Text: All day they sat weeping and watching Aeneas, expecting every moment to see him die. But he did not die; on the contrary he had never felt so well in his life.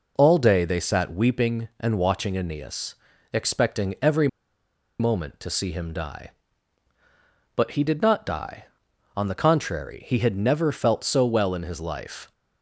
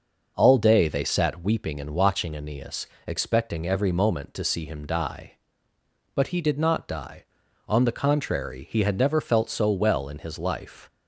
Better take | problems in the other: second | pauses between "every" and "moment"; noticeable; at 4.2 s; 0.72 s long

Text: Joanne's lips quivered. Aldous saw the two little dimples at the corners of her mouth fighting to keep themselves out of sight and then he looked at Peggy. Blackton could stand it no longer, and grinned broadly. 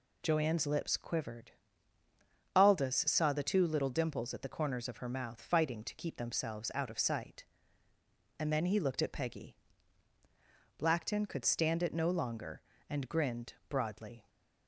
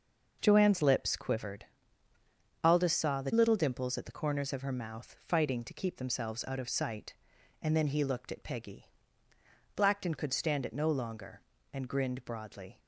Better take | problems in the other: first | skips "two"; at 3.3 s

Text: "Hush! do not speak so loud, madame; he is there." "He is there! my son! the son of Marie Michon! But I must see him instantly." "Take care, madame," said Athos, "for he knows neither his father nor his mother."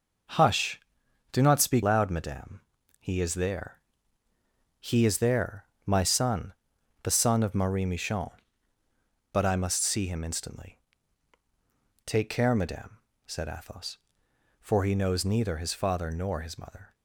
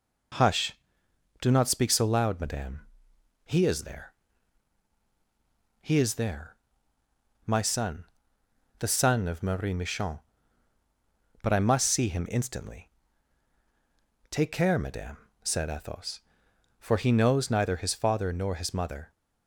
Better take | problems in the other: second | skips "so"; at 1.8 s

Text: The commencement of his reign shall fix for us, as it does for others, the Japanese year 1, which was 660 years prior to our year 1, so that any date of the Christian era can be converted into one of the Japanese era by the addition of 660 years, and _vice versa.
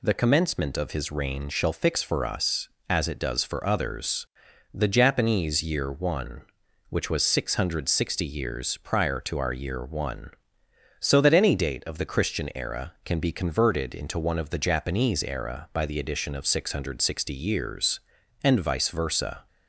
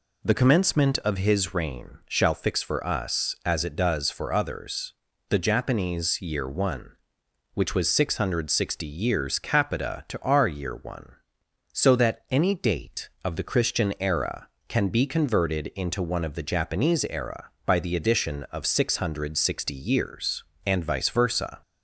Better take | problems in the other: first | says "capita" for "prior"; at 9.3 s

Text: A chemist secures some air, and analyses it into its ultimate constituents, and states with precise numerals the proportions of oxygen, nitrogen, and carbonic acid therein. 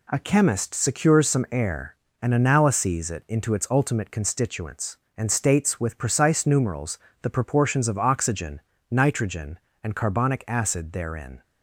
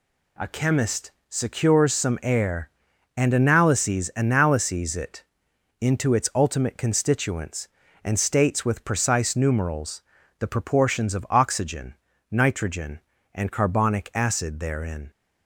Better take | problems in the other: first | pauses between "chemist" and "secures"; slight; at 1.0 s; 0.20 s long // says "analyses" twice; at 4.1 s // pauses between "it" and "into"; noticeable; at 5.2 s; 0.58 s long // pauses between "numerals" and "the"; slight; at 10.0 s; 0.34 s long; slight in the first

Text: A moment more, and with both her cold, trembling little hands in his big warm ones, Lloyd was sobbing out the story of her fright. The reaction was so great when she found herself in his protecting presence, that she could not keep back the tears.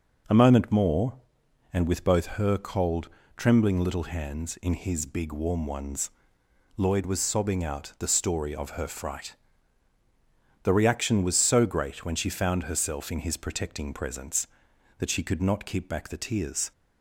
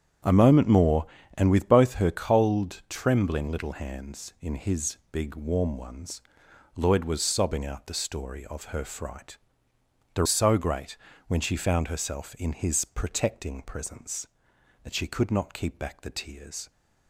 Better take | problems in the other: first | starts louder than the rest; strong; until 1.5 s; 8.5 dB // pauses between "his" and "big"; slight; at 4.9 s; 0.16 s long // skips "reaction was"; at 10.2 s // pauses between "great" and "when"; slight; at 10.9 s; 0.32 s long

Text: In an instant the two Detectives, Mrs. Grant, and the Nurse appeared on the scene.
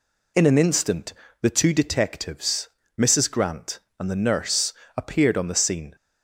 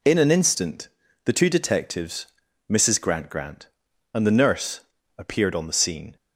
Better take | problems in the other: first | pauses between "instant" and "the"; at 0.8 s; 0.38 s long; slight in the first // says "Grant" twice; at 3.2 s // pauses between "Nurse" and "appeared"; slight; at 4.7 s; 0.36 s long; slight in the first

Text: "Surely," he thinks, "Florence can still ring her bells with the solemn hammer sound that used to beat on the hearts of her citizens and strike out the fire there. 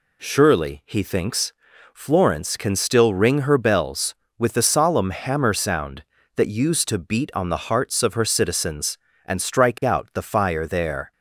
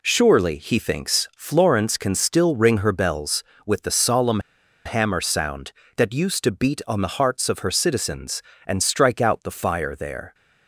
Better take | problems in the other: first | pauses between "solemn" and "hammer"; at 4.4 s; 0.45 s long

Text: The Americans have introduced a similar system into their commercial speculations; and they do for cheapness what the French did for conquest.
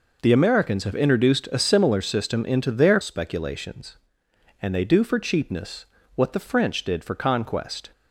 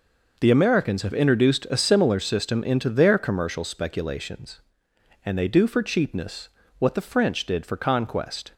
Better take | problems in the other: second | skips "commercial"; at 2.9 s // pauses between "cheapness" and "what"; slight; at 5.8 s; 0.28 s long; slight in the second

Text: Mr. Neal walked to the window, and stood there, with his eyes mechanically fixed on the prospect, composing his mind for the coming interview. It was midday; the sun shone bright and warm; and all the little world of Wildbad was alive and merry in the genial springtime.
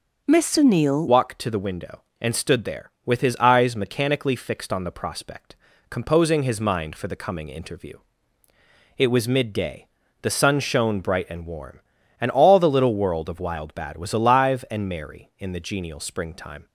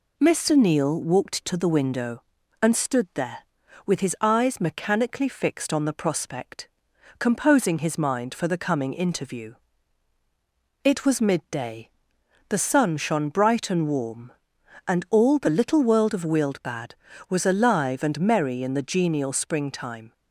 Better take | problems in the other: second | starts louder than the rest; until 1.2 s; 6.5 dB // changes voice at "walked"; from 1.0 s on; 15.6 s long

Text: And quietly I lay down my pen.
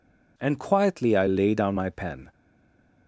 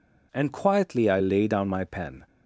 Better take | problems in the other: second | stays silent after the last word; slight; from 2.3 s on; 0.7 s long

